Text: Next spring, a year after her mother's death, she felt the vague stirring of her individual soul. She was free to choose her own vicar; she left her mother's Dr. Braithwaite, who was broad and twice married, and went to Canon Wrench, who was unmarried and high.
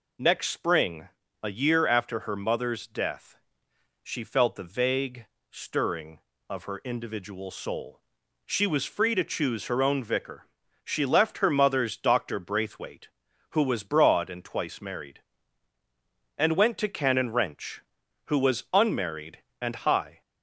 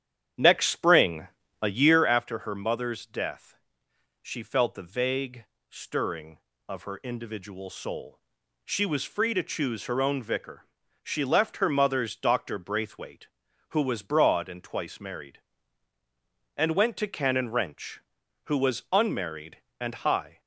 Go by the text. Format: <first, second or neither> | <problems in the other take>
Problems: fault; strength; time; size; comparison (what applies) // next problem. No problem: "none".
first | starts louder than the rest; strong; until 2.2 s; 9.5 dB // pauses between "vague" and "stirring"; slight; at 5.4 s; 0.24 s long; slight in the first